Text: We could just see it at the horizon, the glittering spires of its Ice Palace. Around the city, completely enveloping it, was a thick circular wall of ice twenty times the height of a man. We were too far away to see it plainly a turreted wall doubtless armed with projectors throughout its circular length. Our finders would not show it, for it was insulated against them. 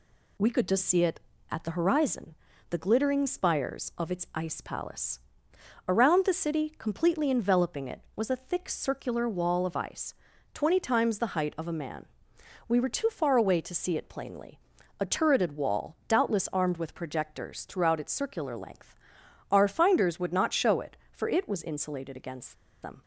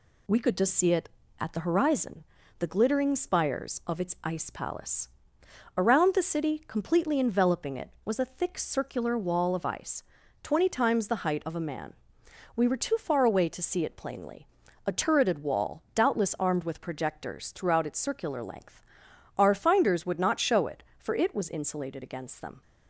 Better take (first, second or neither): second